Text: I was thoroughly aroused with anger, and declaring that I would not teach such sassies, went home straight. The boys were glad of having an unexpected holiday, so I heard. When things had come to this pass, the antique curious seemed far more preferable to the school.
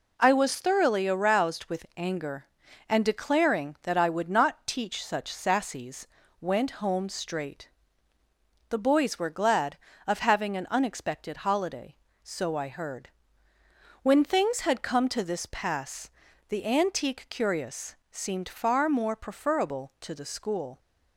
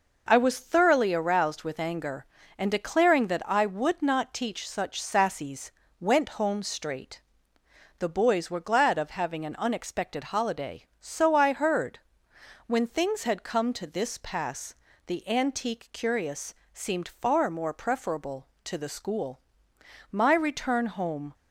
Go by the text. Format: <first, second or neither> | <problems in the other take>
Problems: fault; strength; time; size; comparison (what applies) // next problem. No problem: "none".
first | pauses between "curious" and "seemed"; slight; at 16.5 s; 0.20 s long; slight in the first // goes on to say "My return home"; noticeable; from 20.1 s on; 1.2 s long